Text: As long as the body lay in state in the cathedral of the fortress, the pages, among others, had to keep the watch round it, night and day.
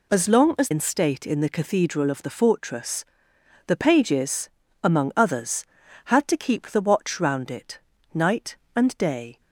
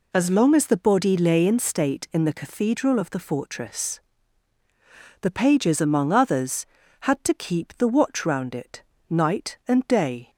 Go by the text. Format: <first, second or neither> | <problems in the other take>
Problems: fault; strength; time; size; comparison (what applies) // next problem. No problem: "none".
second | skips "the body lay"; at 0.7 s